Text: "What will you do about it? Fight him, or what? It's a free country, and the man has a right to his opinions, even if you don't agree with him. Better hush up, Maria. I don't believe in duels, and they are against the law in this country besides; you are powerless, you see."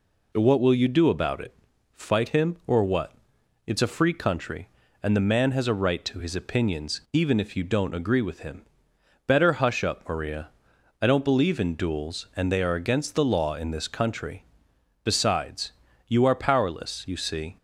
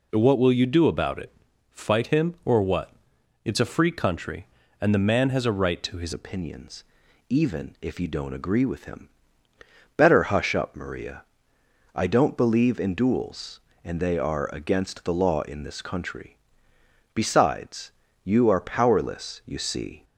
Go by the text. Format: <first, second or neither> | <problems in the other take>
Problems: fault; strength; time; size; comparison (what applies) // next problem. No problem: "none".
first | changes voice at "opinions"; from 6.1 s on; 13.9 s long // pauses between "country" and "besides"; noticeable; at 16.3 s; 0.78 s long; noticeable in the first